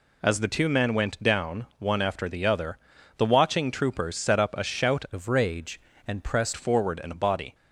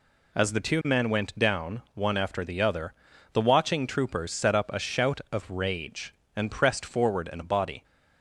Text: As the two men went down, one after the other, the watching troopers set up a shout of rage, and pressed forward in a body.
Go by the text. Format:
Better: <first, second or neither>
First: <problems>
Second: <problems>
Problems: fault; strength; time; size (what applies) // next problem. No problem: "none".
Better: second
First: changes voice from "of" to "pressed"; from 5.1 to 6.5 s; 1.4 s long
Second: none